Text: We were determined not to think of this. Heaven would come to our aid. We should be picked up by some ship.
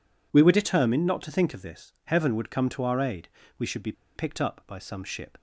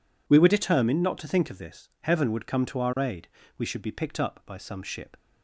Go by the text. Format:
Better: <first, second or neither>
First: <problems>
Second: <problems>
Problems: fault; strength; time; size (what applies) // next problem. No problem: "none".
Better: second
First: pauses between "be" and "picked"; slight; at 3.9 s; 0.23 s long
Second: none